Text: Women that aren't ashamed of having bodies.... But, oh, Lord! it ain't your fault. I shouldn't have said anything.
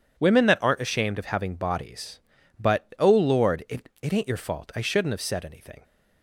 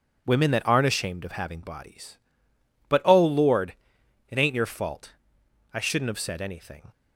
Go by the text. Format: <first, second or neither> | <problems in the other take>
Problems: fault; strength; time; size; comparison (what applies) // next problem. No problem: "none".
second | says "it" twice; at 4.0 s